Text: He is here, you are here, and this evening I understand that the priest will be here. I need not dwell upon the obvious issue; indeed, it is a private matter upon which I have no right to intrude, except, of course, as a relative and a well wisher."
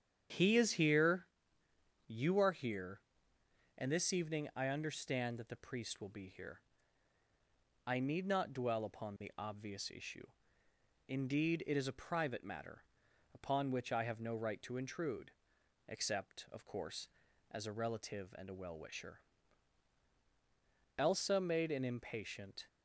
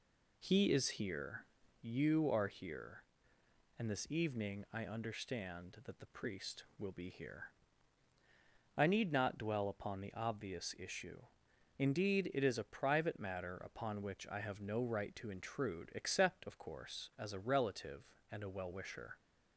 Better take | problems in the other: second | starts louder than the rest; strong; until 2.1 s; 8.5 dB // pauses between "matter" and "upon"; noticeable; at 12.8 s; 0.50 s long // goes on to say "Elsa made an impatient"; from 21.0 s on; 1.6 s long

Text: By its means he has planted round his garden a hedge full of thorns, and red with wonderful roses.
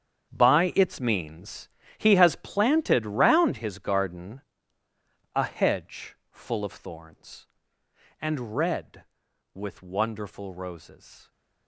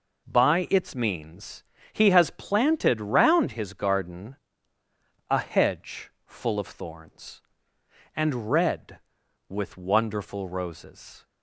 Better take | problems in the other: second | gets quieter; strong; throughout; 13 dB // pauses between "means" and "he"; slight; at 1.6 s; 0.28 s long; slight in the second // pauses between "garden" and "a"; noticeable; at 4.4 s; 0.92 s long; noticeable in the second

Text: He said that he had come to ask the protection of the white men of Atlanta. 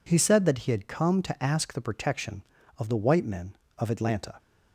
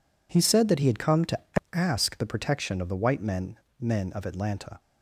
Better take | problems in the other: first | pauses between "to" and "ask"; slight; at 1.3 s; 0.34 s long // says "men" twice; at 3.8 s

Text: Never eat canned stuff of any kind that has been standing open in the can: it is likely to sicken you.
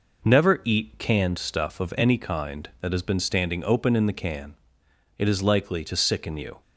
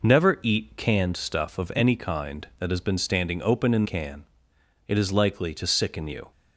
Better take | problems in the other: first | skips "the"; at 3.8 s

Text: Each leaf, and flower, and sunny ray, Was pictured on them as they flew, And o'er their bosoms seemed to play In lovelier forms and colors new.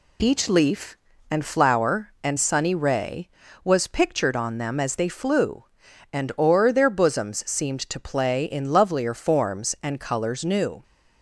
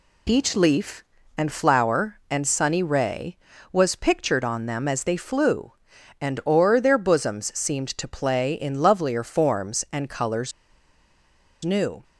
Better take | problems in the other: first | pauses between "colors" and "new"; at 10.5 s; 1.1 s long

